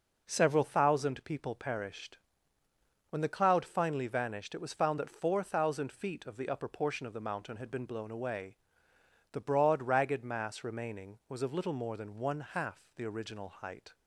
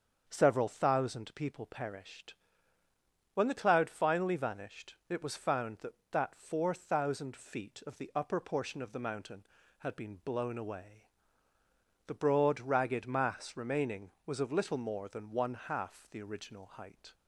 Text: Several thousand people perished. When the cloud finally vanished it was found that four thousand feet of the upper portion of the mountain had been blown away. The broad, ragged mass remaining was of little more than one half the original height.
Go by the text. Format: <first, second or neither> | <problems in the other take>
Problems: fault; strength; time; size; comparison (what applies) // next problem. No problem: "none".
first | starts louder than the rest; until 1.2 s; 7 dB // pauses between "vanished" and "it"; slight; at 4.9 s; 0.16 s long // says "that" twice; at 6.1 s